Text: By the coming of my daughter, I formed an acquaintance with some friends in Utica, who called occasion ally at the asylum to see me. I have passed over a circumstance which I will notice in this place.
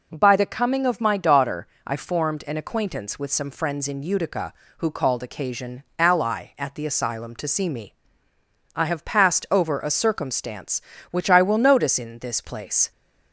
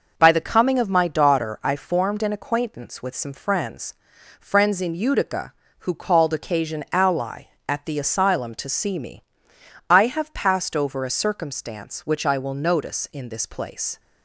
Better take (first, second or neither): first